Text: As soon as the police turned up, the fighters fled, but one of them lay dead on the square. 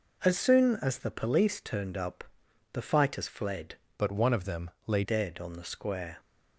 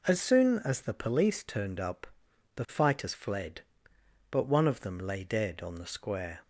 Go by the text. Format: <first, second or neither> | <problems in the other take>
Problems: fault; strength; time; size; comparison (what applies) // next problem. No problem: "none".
second | changes voice from "but" to "lay"; from 3.9 to 5.0 s; 1.1 s long // pauses between "them" and "lay"; slight; at 4.6 s; 0.16 s long